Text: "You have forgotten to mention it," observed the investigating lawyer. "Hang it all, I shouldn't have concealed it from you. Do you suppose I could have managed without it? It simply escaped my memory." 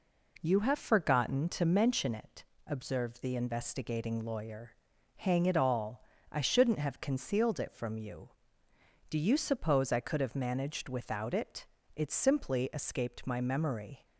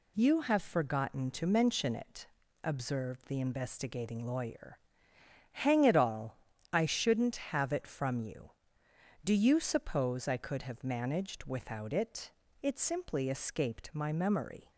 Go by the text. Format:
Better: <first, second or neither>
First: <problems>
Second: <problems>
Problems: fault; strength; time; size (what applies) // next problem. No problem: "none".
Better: first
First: none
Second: skips "concealed"; at 7.7 s